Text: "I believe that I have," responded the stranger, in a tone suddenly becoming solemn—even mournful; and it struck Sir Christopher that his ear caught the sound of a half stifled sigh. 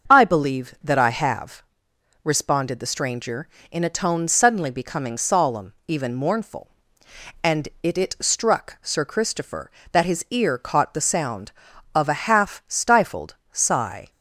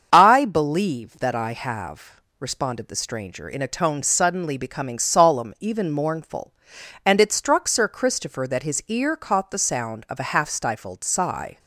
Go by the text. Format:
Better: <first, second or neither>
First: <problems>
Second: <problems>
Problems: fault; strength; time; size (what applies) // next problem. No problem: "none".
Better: second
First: starts louder than the rest; until 1.1 s; 6.5 dB // says "it" twice; at 7.9 s // pauses between "stifled" and "sigh"; slight; at 13.3 s; 0.16 s long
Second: starts louder than the rest; until 1.1 s; 7 dB